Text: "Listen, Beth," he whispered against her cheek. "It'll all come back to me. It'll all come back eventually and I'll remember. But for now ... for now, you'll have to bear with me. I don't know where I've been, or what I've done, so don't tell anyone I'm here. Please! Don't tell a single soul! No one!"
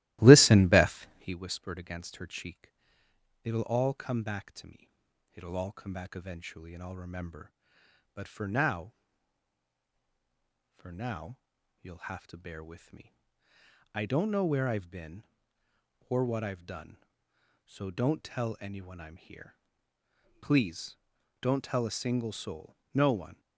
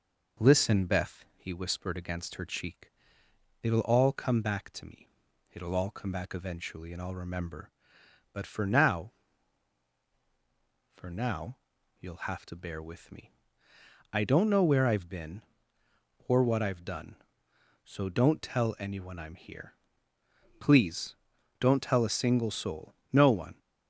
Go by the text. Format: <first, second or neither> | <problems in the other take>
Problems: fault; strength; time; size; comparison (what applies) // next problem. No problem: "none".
second | starts louder than the rest; strong; until 1.4 s; 16 dB